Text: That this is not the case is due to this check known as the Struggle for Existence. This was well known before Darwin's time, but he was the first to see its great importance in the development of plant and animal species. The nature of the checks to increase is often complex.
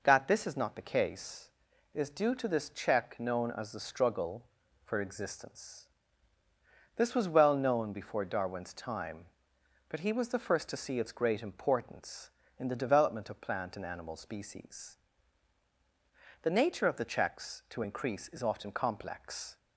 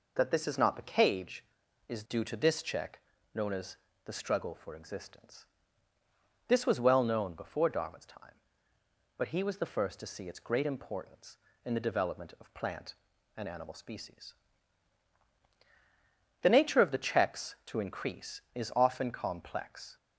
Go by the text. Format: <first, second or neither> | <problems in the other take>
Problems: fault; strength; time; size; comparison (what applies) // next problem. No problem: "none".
first | says "cage" for "case"; at 0.9 s // pauses between "check" and "known"; slight; at 2.9 s; 0.36 s long // pauses between "as" and "the"; slight; at 3.7 s; 0.28 s long